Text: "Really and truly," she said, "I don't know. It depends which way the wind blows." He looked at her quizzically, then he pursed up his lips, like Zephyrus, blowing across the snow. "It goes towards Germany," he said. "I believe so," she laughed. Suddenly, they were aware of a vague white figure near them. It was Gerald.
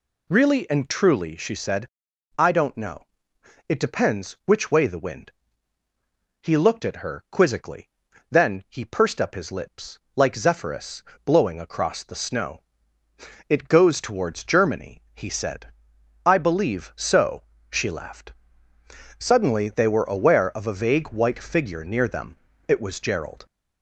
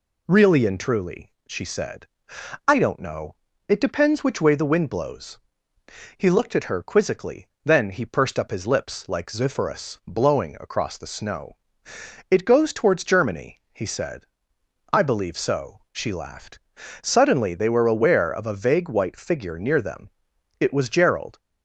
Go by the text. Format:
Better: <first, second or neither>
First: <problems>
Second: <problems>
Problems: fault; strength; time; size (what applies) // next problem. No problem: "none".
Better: second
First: skips "blows"; at 5.8 s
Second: none